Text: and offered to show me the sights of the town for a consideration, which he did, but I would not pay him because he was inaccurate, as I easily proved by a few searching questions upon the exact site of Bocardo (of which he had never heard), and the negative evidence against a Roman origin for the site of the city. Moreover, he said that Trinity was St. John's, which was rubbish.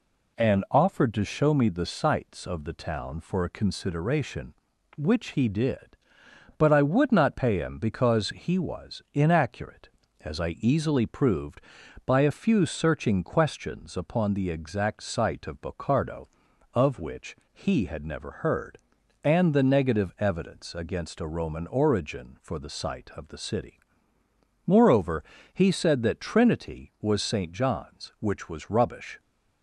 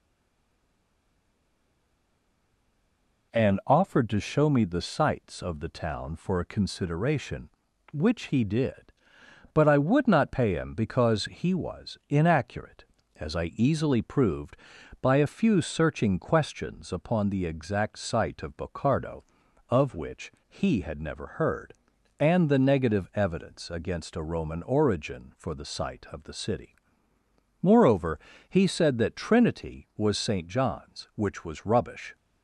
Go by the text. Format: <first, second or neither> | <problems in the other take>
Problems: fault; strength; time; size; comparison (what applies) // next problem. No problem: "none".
first | stays silent before the first word; strong; until 3.3 s; 3.3 s long // pauses between "which" and "he"; slight; at 20.3 s; 0.16 s long; slight in the first